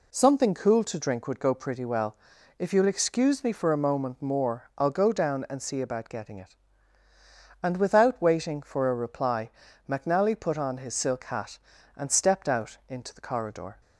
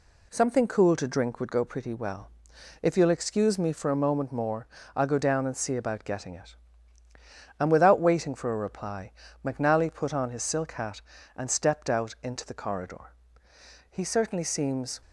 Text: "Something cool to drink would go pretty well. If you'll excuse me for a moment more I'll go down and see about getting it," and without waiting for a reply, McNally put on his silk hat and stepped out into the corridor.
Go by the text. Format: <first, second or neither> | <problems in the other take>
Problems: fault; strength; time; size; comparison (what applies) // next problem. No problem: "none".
first | pauses between "more" and "I'll"; slight; at 4.6 s; 0.28 s long // goes on to say "He certainly seems"; noticeable; from 13.8 s on; 1.1 s long